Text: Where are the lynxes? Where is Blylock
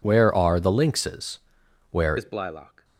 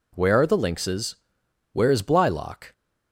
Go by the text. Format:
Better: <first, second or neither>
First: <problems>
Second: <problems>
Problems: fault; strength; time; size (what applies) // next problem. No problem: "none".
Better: second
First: changes voice at "is"; from 2.1 s on; 0.7 s long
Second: none